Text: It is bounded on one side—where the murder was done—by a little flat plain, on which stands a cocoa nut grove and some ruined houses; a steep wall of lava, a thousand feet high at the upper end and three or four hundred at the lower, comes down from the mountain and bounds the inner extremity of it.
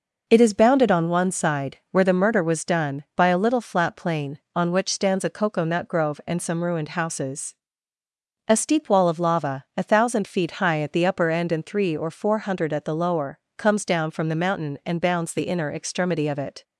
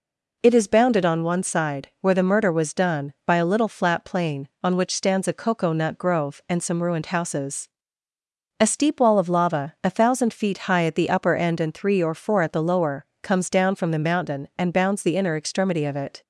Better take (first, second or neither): first